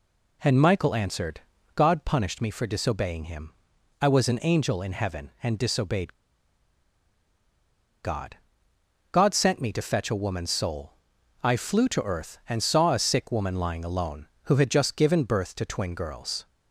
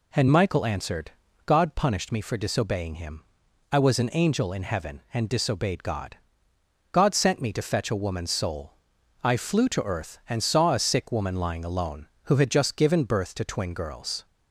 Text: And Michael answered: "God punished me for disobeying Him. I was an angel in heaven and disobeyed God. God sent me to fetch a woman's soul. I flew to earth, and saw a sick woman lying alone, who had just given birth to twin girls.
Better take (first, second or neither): second